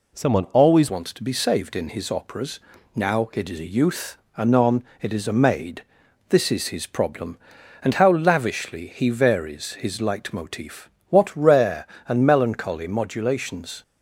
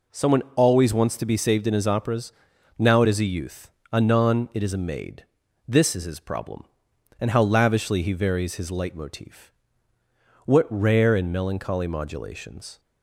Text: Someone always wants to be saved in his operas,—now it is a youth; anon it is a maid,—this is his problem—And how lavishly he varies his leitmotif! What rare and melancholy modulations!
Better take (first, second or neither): second